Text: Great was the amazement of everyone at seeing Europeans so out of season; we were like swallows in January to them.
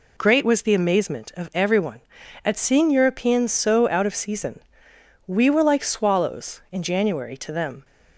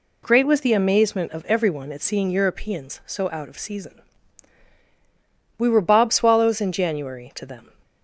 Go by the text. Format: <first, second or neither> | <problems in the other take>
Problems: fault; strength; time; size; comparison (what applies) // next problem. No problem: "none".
first | says "bob" for "like"; at 5.8 s